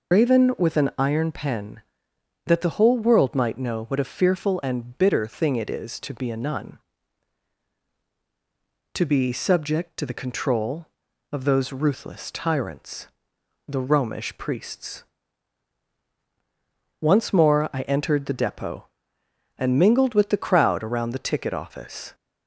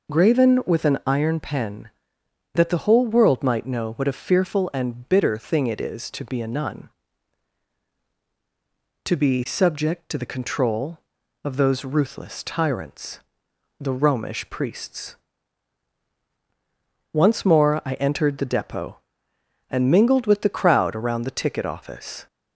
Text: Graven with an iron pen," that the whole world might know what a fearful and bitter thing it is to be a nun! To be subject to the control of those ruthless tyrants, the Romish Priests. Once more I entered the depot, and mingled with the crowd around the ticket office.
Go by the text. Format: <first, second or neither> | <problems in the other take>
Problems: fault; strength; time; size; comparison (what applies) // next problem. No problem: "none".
second | loses the start of "Graven"; at 0.1 s; 100 ms